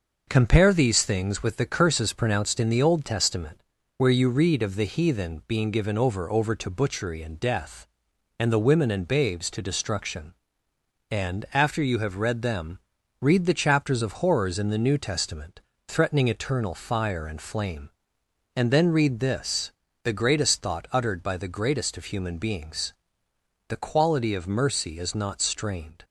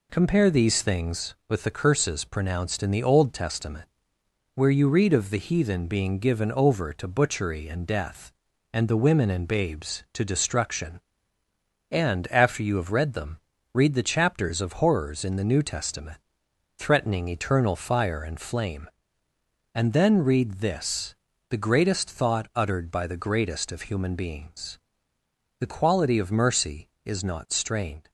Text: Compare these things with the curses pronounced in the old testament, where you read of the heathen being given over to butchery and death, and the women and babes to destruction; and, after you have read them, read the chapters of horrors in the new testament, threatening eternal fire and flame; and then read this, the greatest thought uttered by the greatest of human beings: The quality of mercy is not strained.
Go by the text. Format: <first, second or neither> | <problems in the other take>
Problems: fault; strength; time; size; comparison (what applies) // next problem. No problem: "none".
second | says "over" twice; at 6.2 s